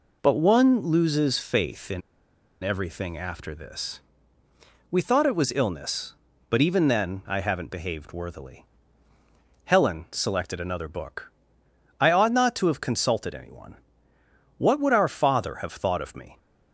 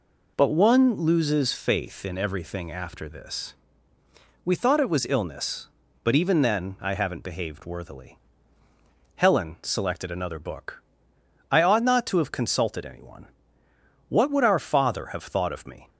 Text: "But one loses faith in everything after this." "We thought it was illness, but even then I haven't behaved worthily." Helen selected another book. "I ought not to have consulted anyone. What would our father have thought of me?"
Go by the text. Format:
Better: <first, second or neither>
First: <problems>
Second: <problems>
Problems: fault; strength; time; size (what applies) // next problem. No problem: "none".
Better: second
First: pauses between "in" and "everything"; noticeable; at 2.0 s; 0.62 s long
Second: none